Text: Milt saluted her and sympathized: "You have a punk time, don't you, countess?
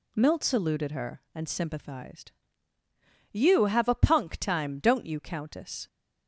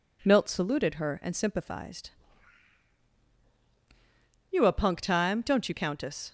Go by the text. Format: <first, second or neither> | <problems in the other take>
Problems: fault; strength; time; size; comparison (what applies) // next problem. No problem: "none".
first | skips "have"; at 4.6 s